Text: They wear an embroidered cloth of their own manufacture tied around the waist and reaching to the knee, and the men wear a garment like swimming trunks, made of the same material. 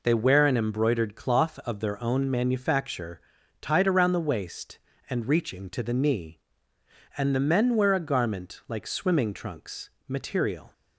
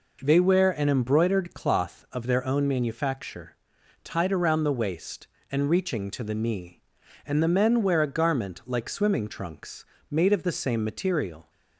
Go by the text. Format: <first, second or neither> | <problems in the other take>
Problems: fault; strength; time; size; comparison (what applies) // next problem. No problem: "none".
second | pauses between "manufacture" and "tied"; at 3.2 s; 0.40 s long; noticeable in the second // skips "made of the same"; at 9.9 s